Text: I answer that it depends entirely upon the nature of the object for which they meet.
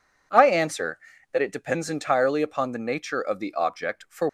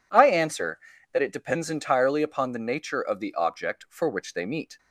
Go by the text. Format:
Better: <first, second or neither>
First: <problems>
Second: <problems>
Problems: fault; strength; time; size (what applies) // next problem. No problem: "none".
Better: second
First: stops before "which they meet"; at 4.2 s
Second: none